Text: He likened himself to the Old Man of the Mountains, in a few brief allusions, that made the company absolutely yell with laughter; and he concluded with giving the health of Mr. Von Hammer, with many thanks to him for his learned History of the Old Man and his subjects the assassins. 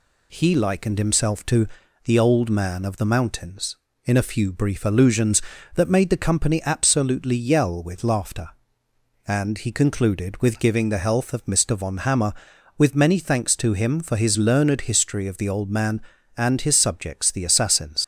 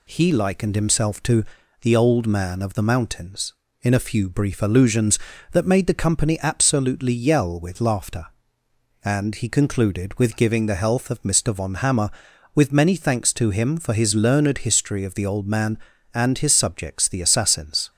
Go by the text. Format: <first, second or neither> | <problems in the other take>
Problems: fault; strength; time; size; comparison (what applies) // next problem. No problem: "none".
second | pauses between "to" and "the"; at 1.6 s; 0.38 s long; also in the second // leaves "assassins" unfinished; at 18.0 s; 85 ms